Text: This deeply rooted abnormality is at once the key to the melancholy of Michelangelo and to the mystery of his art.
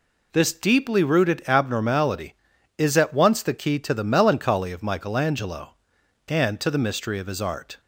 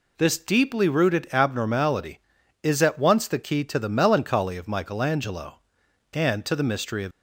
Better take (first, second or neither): first